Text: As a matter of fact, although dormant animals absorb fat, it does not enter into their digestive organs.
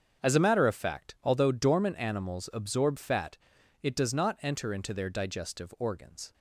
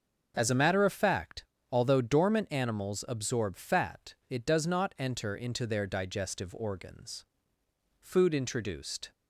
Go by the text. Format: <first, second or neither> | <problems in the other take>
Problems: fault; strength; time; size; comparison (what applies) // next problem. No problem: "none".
first | starts louder than the rest; until 1.3 s; 6.5 dB; also in the first // goes on to say "Food introduced"; noticeable; from 8.0 s on; 1.1 s long